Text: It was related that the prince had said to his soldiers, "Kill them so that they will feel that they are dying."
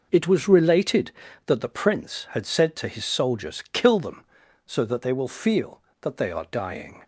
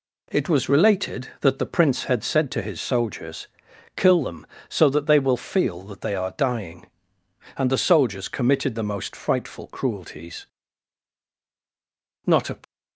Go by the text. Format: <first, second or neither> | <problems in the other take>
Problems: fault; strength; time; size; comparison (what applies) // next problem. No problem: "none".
first | goes on to say "And the soldiers committed the most frightful cruelties Not a"; strong; from 7.5 s on; 5.0 s long